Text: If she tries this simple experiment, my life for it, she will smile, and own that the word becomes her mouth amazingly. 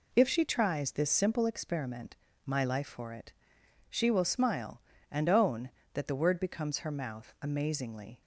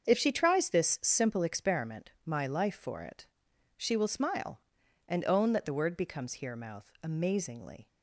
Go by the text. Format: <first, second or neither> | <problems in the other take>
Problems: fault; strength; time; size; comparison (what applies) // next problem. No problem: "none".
first | starts louder than the rest; until 1.0 s; 7 dB // says "here" for "her"; at 6.3 s